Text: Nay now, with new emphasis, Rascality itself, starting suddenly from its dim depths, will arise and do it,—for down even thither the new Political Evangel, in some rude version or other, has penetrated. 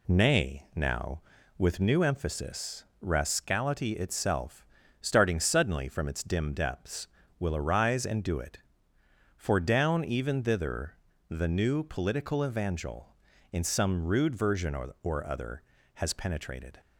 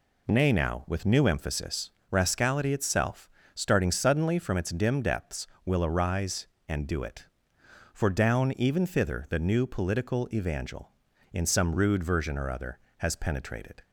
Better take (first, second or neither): second